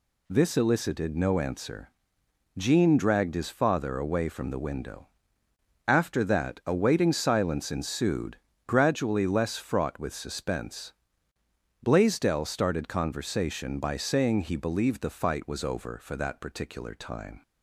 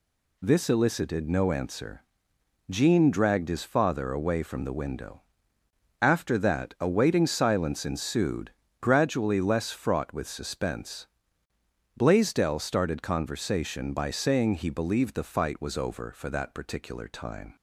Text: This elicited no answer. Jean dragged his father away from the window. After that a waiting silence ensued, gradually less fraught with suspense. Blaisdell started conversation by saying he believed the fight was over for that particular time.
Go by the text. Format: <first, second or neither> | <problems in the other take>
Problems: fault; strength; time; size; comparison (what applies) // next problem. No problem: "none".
neither | none